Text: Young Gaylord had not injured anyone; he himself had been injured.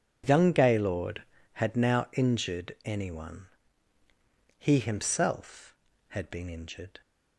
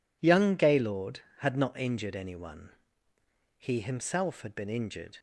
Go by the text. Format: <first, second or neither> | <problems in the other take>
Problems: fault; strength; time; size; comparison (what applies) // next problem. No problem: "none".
second | says "now" for "not"; at 1.7 s